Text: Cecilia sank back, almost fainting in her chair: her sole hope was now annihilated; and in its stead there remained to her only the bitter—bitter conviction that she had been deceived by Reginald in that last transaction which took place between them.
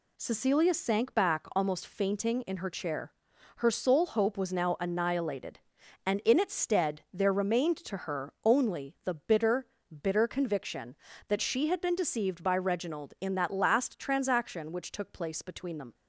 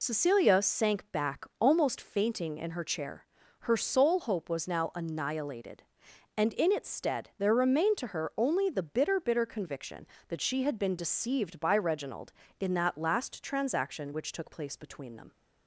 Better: first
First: none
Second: loses the start of "Cecilia"; at 0.0 s; 55 ms

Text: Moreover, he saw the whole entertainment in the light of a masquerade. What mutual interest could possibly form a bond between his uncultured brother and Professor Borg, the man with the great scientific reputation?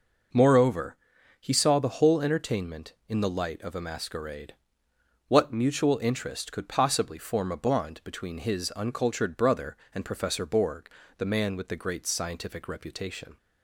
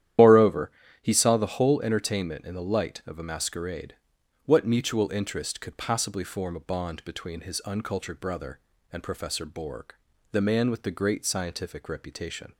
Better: first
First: none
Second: loses the start of "Moreover"; at 0.1 s; 65 ms // starts louder than the rest; strong; until 1.5 s; 11.5 dB

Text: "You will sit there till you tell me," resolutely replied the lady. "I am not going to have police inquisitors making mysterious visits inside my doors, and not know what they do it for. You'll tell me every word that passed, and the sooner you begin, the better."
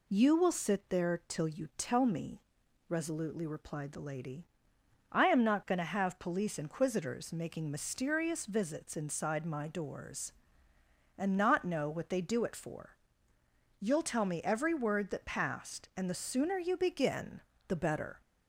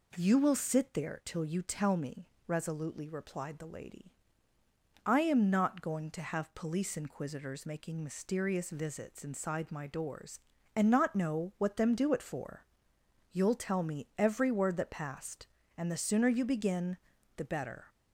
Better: first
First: none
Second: says "them" for "they"; at 11.7 s

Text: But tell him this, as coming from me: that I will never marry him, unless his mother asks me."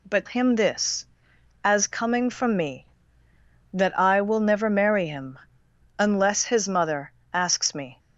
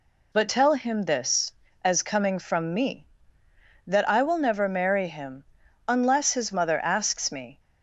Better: second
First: skips "tell"; at 0.2 s // pauses between "mother" and "asks"; slight; at 7.1 s; 0.22 s long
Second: none

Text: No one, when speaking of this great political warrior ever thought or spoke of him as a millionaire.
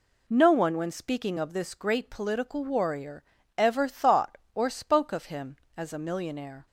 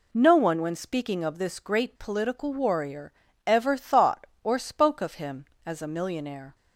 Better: neither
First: pauses between "warrior" and "ever"; slight; at 3.2 s; 0.34 s long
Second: pauses between "warrior" and "ever"; slight; at 3.1 s; 0.34 s long

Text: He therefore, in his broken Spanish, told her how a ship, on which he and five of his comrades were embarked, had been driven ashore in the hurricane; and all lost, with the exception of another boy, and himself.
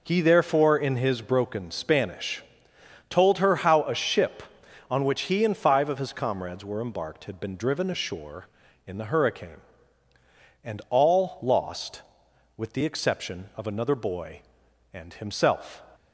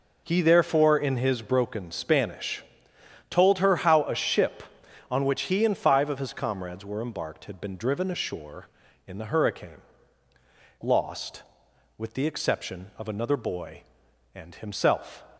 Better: first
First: none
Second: skips "and all"; at 10.3 s

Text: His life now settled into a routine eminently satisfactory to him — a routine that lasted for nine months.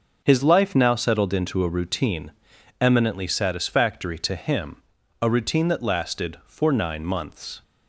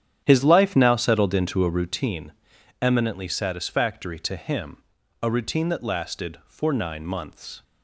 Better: first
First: pauses between "routine" and "eminently"; noticeable; at 2.3 s; 0.50 s long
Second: starts louder than the rest; strong; until 2.0 s; 9.5 dB // pauses between "routine" and "eminently"; noticeable; at 2.3 s; 0.50 s long

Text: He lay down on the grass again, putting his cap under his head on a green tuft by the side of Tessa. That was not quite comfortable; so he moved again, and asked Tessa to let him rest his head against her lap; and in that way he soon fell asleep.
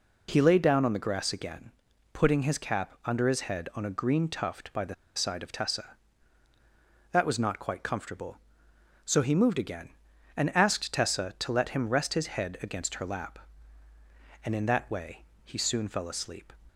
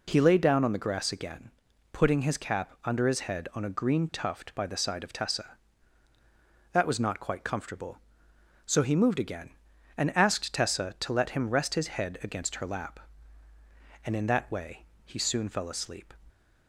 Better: second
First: pauses between "the" and "side"; slight; at 4.9 s; 0.22 s long // pauses between "way" and "he"; slight; at 15.2 s; 0.22 s long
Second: pauses between "way" and "he"; slight; at 14.8 s; 0.22 s long

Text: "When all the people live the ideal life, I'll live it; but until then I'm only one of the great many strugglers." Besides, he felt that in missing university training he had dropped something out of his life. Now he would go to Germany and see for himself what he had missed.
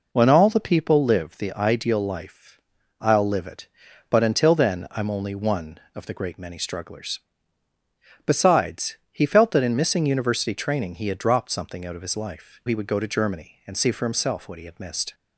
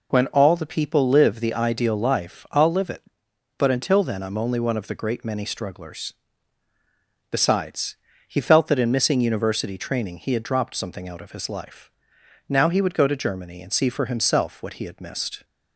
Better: second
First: skips "Now"; at 12.6 s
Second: none

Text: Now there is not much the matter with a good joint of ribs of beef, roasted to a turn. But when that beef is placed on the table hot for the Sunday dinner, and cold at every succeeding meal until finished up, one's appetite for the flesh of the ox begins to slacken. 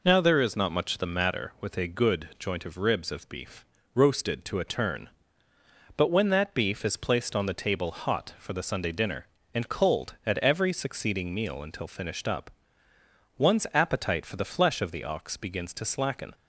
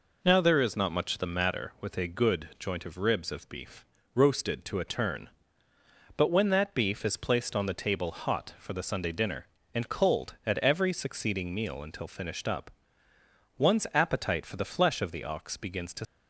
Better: first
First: none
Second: stops before "slacken"; at 16.0 s

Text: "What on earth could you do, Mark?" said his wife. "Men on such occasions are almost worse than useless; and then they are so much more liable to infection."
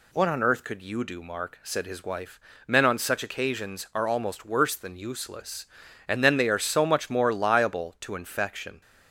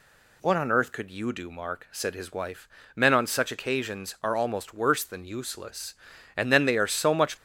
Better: first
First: none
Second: stops before "more liable to infection"; at 7.3 s

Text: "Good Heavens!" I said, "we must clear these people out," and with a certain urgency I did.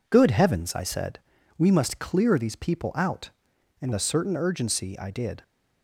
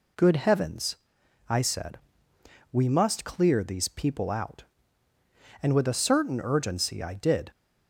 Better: second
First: skips "with"; at 3.9 s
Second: none

